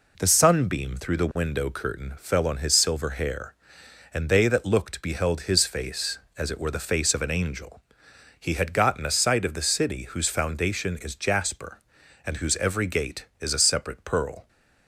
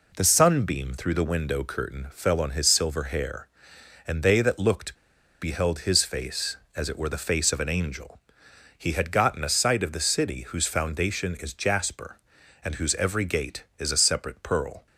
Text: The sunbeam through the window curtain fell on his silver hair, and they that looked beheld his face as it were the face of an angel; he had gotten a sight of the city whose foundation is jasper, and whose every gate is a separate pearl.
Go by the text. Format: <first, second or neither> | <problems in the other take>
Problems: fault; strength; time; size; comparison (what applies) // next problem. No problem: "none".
first | pauses between "looked" and "beheld"; noticeable; at 4.9 s; 0.47 s long